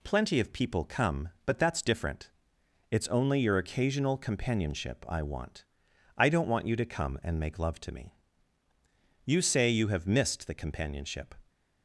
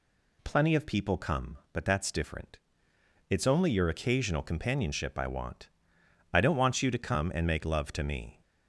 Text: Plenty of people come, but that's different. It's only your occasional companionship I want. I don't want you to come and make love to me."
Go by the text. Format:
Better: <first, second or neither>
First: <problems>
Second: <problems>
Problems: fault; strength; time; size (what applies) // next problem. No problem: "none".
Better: second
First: goes on to say "You say you have missed the companionship"; strong; from 9.2 s on; 2.1 s long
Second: none